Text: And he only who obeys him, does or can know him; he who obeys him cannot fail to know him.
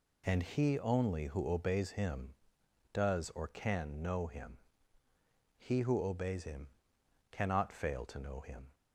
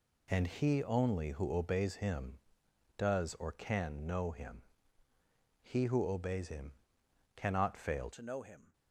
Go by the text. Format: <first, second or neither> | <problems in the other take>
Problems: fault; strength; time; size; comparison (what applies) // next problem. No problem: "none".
first | pauses between "him" and "cannot"; noticeable; at 6.7 s; 0.62 s long; noticeable in the first // changes voice at "to"; from 8.1 s on; 0.6 s long